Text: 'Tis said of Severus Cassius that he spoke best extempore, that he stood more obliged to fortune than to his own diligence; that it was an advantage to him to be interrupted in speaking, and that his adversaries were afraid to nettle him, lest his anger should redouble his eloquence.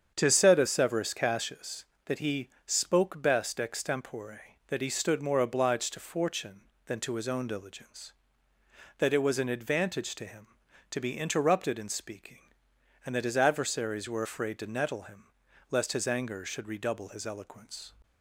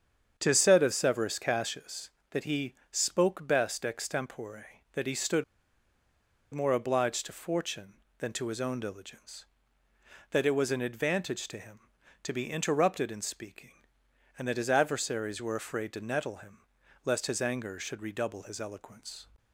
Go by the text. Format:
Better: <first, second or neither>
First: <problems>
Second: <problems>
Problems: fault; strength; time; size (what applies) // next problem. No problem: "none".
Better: first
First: starts louder than the rest; strong; until 1.1 s; 7.5 dB // pauses between "he" and "spoke"; slight; at 2.4 s; 0.16 s long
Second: starts louder than the rest; strong; until 1.3 s; 7.5 dB // pauses between "he" and "spoke"; slight; at 2.7 s; 0.16 s long // pauses between "stood" and "more"; at 5.4 s; 1.1 s long